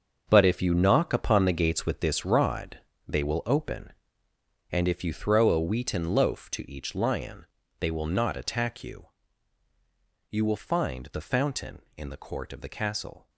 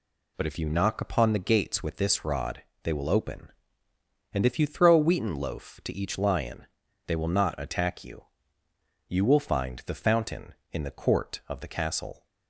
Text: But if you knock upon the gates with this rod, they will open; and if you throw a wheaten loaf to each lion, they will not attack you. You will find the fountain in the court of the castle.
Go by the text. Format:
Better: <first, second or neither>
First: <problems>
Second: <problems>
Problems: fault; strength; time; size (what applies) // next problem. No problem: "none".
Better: second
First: gets quieter; strong; throughout; 11 dB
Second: none